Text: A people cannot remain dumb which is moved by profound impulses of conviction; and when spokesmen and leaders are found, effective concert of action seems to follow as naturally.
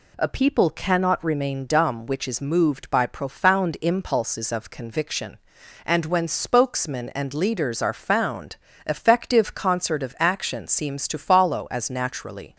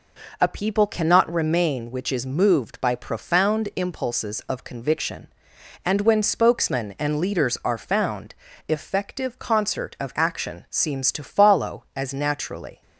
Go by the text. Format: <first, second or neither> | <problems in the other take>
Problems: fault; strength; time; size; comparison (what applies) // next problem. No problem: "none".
first | skips "dumb"; at 1.9 s